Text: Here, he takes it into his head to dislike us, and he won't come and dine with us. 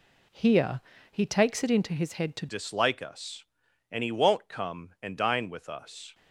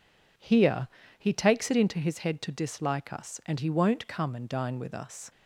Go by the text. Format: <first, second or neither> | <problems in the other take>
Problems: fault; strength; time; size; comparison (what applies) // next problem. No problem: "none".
second | changes voice at "dislike"; from 2.4 s on; 3.7 s long